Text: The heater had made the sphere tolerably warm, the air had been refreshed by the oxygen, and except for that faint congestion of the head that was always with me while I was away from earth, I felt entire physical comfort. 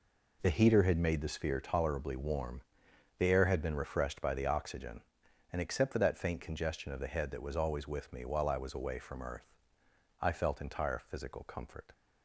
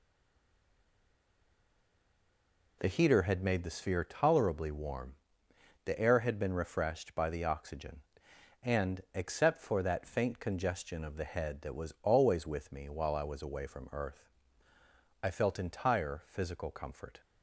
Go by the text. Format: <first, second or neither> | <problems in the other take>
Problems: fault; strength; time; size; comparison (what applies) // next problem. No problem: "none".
first | stays silent before the first word; strong; until 2.8 s; 2.8 s long